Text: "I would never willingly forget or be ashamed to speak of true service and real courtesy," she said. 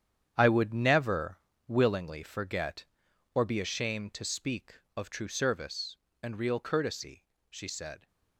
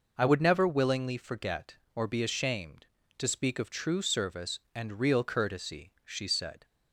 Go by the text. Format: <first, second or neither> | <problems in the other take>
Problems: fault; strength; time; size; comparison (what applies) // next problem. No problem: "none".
second | gets quieter; strong; throughout; 10.5 dB // pauses between "never" and "willingly"; slight; at 1.3 s; 0.28 s long